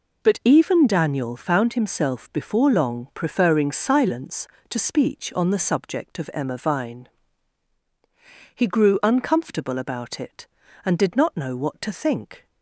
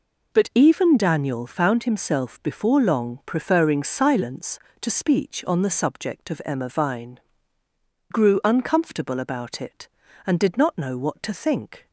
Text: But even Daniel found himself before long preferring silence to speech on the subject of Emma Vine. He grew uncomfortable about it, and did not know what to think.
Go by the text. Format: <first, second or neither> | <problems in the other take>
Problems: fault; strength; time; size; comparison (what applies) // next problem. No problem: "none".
first | skips "He"; at 7.6 s